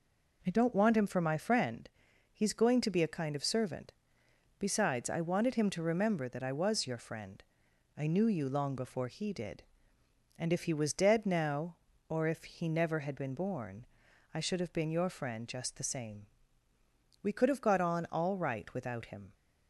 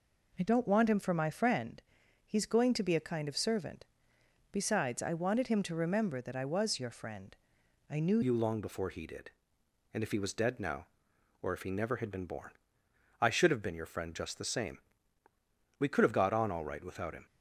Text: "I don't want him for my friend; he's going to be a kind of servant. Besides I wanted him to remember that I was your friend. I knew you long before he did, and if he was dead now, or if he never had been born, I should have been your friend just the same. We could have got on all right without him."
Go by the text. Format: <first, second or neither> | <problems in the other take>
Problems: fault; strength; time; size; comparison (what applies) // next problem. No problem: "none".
first | changes voice at "you"; from 8.2 s on; 9.0 s long